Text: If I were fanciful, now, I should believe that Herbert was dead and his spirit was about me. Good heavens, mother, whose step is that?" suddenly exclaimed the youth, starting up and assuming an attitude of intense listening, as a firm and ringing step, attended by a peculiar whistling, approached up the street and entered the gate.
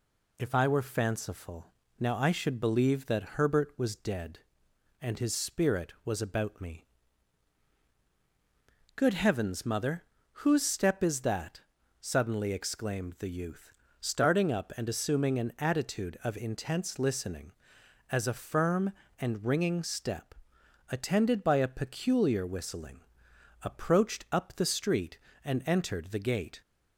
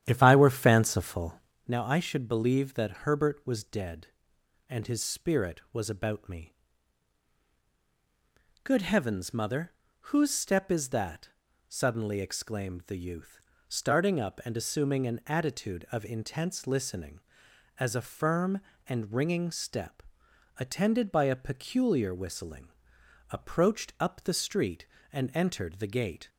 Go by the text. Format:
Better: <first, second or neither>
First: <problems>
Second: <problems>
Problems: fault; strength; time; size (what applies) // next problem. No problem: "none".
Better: first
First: none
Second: starts louder than the rest; strong; until 1.7 s; 10.5 dB